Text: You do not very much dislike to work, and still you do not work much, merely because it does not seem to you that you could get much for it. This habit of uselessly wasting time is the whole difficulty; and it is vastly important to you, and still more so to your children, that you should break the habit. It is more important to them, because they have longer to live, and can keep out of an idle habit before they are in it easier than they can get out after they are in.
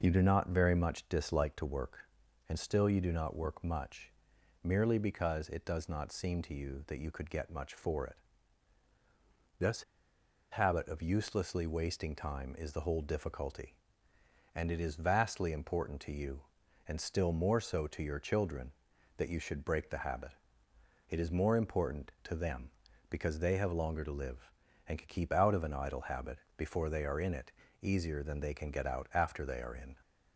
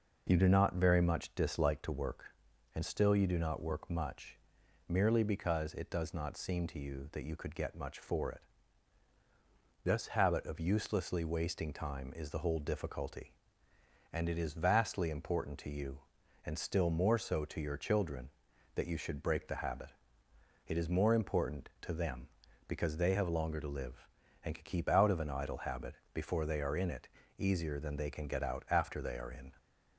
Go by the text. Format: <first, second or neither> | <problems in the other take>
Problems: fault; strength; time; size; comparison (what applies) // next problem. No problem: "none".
second | pauses between "This" and "habit"; noticeable; at 9.8 s; 0.67 s long // pauses between "habit" and "before"; slight; at 26.3 s; 0.22 s long; slight in the second // pauses between "it" and "easier"; slight; at 27.5 s; 0.28 s long; slight in the second